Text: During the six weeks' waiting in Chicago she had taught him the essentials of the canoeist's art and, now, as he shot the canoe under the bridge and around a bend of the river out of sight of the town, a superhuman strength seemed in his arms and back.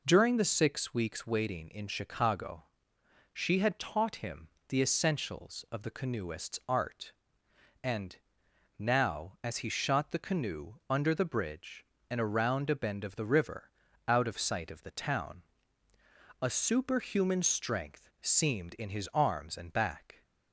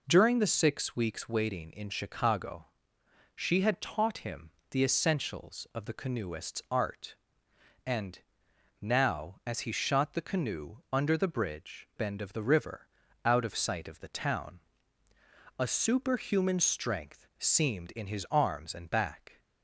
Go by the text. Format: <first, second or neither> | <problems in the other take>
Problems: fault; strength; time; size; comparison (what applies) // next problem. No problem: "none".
first | pauses between "Chicago" and "she"; noticeable; at 2.6 s; 0.68 s long; noticeable in the first // pauses between "him" and "the"; slight; at 4.5 s; 0.20 s long; slight in the first // pauses between "canoe" and "under"; slight; at 10.7 s; 0.16 s long; slight in the first // skips "and around a"; at 11.9 s // pauses between "river" and "out"; at 12.8 s; 0.38 s long; also in the first